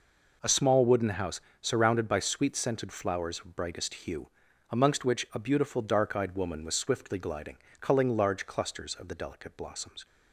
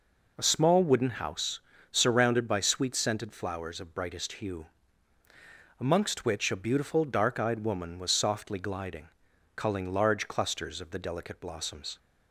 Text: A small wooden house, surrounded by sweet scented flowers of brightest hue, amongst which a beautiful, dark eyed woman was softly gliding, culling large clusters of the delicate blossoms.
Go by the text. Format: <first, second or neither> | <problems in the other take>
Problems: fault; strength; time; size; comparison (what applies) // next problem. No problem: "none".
second | says "swiftly" for "softly"; at 6.7 s